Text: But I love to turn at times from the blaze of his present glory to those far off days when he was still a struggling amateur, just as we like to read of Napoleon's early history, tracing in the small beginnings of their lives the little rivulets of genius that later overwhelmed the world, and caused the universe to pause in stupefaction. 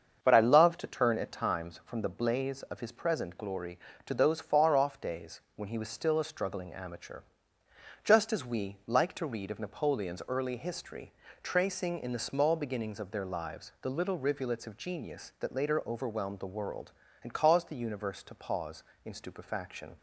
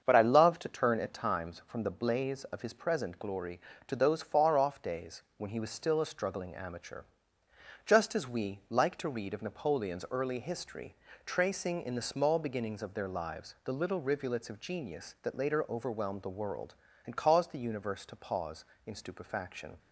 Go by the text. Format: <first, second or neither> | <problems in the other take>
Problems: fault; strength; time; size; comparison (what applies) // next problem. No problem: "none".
neither | starts louder than the rest; the same in both